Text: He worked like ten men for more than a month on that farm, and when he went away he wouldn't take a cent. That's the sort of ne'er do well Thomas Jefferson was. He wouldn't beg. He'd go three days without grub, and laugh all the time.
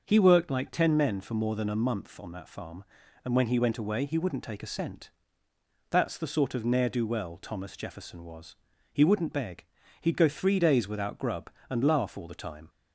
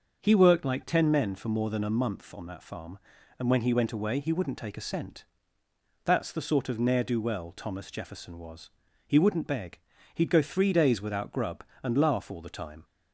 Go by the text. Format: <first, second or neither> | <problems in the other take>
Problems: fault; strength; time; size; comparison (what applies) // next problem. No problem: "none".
neither | starts louder than the rest; the same in both